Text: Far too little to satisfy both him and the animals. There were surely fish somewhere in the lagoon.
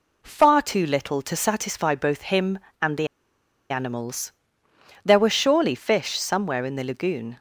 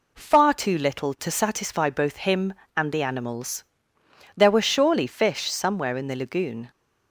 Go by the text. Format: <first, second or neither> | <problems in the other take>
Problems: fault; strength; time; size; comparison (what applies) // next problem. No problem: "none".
second | pauses between "the" and "animals"; noticeable; at 3.0 s; 0.63 s long